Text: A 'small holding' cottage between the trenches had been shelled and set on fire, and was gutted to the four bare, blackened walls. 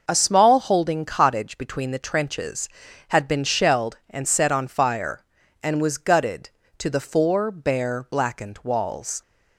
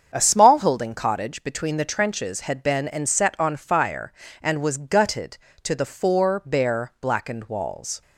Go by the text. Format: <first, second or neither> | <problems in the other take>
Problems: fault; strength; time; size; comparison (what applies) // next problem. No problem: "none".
first | starts louder than the rest; strong; until 1.1 s; 7 dB // skips "shelled"; at 2.8 s